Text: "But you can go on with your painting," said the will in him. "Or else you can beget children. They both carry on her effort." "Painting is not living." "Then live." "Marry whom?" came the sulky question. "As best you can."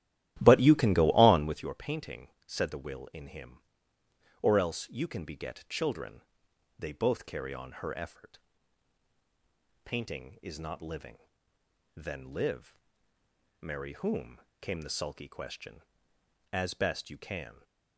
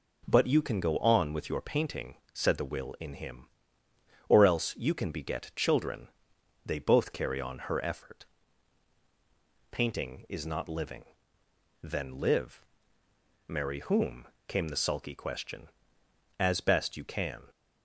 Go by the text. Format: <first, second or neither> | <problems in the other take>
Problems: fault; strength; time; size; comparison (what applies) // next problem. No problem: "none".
second | starts louder than the rest; strong; until 1.7 s; 13.5 dB